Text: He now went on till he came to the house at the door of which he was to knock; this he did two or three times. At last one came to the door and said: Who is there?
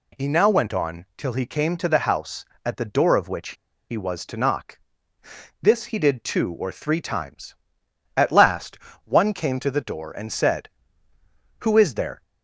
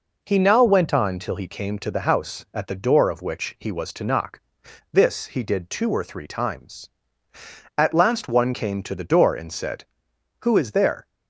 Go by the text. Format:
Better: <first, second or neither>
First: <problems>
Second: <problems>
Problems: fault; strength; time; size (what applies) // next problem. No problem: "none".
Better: second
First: pauses between "which" and "he"; slight; at 3.5 s; 0.35 s long // pauses between "last" and "one"; slight; at 8.7 s; 0.26 s long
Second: none